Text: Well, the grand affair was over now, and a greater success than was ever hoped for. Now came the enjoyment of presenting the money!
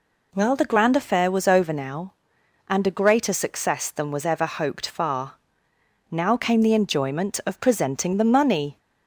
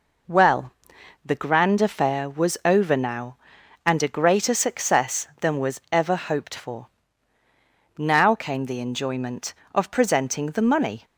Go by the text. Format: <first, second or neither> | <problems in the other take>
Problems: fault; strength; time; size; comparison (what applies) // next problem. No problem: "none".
second | says "far" for "for"; at 4.8 s